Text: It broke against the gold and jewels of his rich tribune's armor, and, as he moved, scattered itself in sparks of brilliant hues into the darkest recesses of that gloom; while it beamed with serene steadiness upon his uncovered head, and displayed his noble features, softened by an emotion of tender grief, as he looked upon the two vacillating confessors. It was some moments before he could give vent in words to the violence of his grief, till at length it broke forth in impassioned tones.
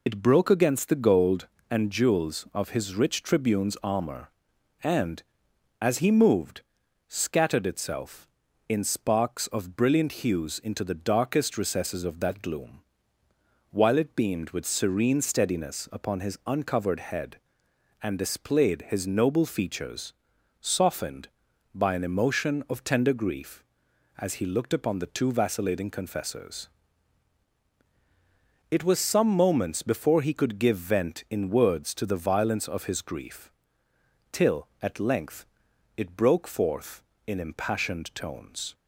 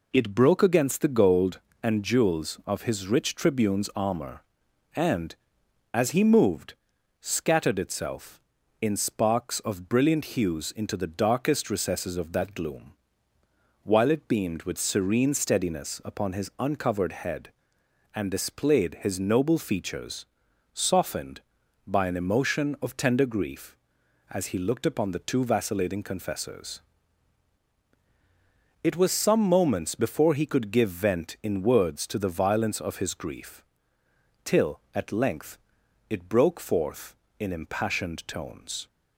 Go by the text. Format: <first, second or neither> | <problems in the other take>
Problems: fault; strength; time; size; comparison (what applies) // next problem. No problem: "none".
second | loses the start of "It"; at 0.0 s; 55 ms // pauses between "length" and "it"; noticeable; at 35.4 s; 0.52 s long; noticeable in the second